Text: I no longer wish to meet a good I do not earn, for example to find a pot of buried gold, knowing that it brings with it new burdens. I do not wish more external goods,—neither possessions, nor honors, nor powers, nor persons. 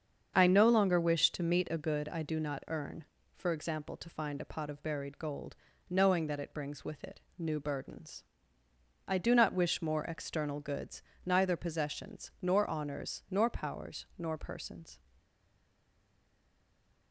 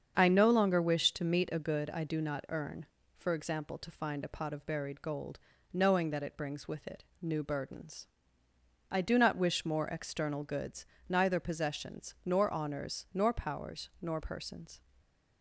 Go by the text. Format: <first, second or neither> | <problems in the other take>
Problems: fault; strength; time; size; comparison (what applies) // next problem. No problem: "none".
second | starts louder than the rest; until 1.3 s; 7 dB; strong in the second // pauses between "it" and "new"; slight; at 7.2 s; 0.16 s long; slight in the second // stays silent after the last word; noticeable; from 15.1 s on; 2.0 s long